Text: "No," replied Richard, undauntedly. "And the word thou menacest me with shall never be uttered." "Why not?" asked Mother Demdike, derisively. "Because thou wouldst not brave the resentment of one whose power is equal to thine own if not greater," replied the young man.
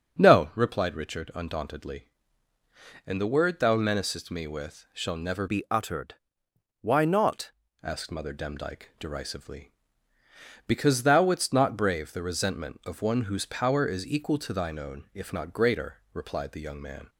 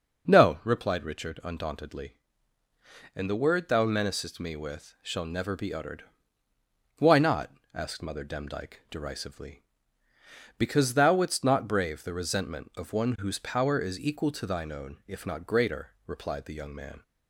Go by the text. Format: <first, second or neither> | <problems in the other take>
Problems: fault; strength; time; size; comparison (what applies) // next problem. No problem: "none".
second | starts louder than the rest; until 1.2 s; 6.5 dB // changes voice from "be" to "not"; from 5.4 to 7.5 s; 2.1 s long